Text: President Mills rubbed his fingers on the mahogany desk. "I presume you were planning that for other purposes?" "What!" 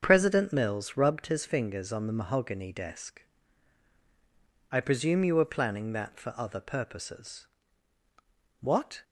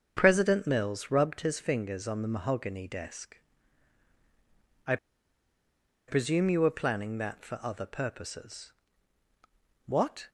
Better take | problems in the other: first | starts louder than the rest; until 1.1 s; 6.5 dB; also in the first // pauses between "I" and "presume"; at 4.9 s; 1.1 s long

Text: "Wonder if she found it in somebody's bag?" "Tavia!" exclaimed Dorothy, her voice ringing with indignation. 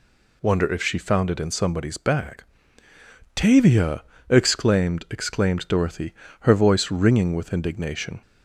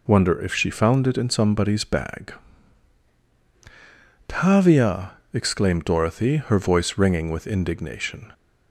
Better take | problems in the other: second | says "exclaimed" twice; at 5.0 s

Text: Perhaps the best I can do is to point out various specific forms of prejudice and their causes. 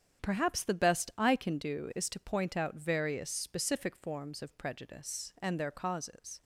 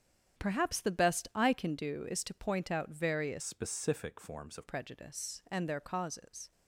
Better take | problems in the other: first | starts louder than the rest; strong; until 1.4 s; 8.5 dB; strong in the first // changes voice from "specific" to "of"; from 3.4 to 4.6 s; 1.2 s long

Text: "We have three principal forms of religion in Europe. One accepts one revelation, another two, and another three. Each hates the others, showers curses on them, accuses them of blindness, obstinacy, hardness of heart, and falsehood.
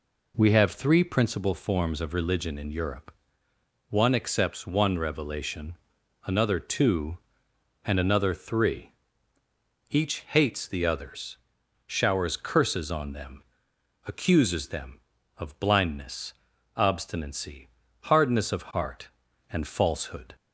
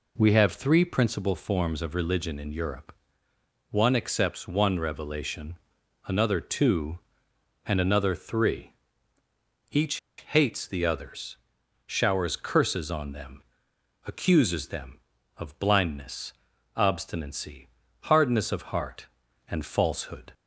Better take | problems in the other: first | pauses between "Each" and "hates"; slight; at 9.9 s; 0.21 s long

